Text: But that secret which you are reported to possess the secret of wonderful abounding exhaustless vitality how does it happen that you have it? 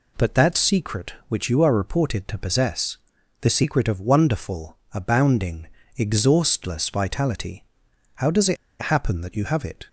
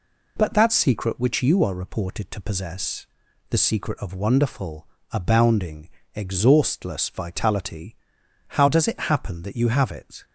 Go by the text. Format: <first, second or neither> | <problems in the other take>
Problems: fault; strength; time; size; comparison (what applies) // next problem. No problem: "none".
second | pauses between "possess" and "the"; at 2.9 s; 0.44 s long; also in the second // pauses between "wonderful" and "abounding"; slight; at 4.7 s; 0.16 s long; slight in the second // pauses between "abounding" and "exhaustless"; slight; at 5.6 s; 0.30 s long; slight in the second // pauses between "vitality" and "how"; noticeable; at 7.6 s; 0.50 s long; noticeable in the second // pauses between "it" and "happen"; slight; at 8.5 s; 0.25 s long